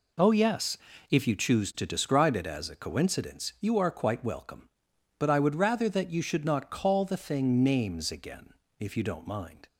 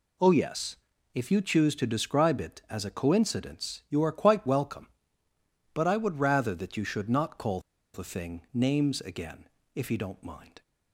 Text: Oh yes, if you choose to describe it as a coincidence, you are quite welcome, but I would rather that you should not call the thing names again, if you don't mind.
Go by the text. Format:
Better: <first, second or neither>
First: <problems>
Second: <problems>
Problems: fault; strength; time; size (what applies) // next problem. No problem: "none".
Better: first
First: none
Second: pauses between "call" and "the"; slight; at 7.5 s; 0.34 s long